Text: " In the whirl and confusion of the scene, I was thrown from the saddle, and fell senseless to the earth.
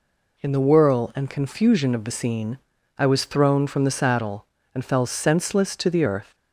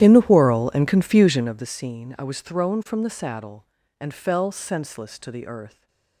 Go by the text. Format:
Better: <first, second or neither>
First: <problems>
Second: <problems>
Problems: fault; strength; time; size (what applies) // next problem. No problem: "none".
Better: first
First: none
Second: starts louder than the rest; strong; until 1.6 s; 11.5 dB // stays silent after the last word; slight; from 5.6 s on; 0.6 s long